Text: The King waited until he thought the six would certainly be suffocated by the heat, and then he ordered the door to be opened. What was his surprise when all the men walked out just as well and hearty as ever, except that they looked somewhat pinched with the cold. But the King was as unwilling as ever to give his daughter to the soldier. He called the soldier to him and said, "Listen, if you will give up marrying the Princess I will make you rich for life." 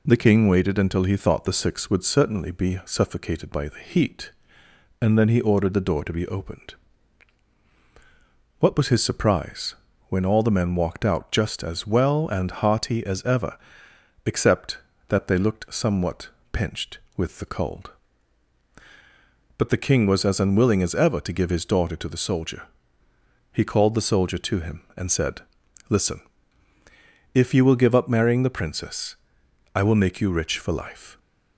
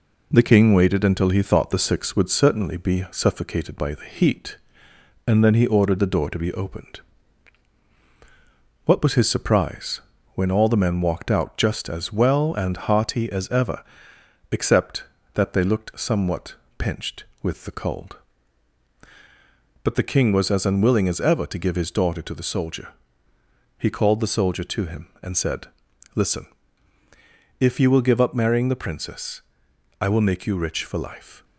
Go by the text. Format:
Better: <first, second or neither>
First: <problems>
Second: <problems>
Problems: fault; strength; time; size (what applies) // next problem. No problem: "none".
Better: first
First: pauses between "surprise" and "when"; slight; at 9.7 s; 0.34 s long // pauses between "somewhat" and "pinched"; slight; at 16.2 s; 0.24 s long // pauses between "Princess" and "I"; noticeable; at 29.1 s; 0.58 s long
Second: gets quieter; slight; throughout; 2.5 dB // pauses between "surprise" and "when"; slight; at 9.9 s; 0.34 s long // pauses between "somewhat" and "pinched"; slight; at 16.5 s; 0.24 s long // pauses between "Princess" and "I"; noticeable; at 29.4 s; 0.58 s long